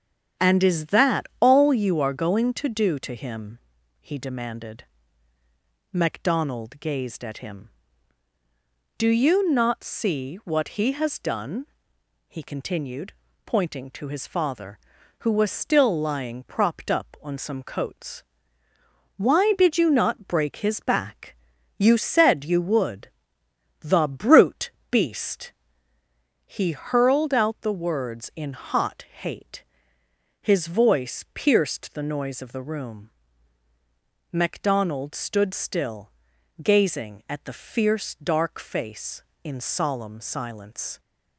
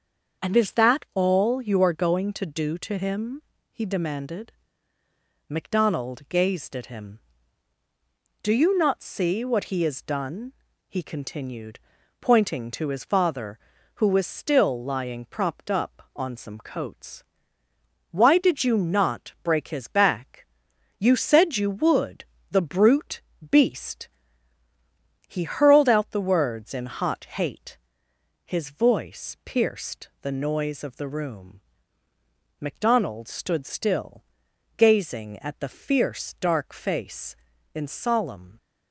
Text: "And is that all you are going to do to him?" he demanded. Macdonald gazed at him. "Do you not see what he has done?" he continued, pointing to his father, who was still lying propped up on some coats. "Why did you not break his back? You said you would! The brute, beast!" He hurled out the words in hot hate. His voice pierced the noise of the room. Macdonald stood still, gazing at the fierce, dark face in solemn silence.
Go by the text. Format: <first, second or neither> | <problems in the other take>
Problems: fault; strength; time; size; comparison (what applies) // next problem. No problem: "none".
first | starts louder than the rest; until 1.4 s; 6.5 dB; strong in the first // stops before "silence"; at 38.5 s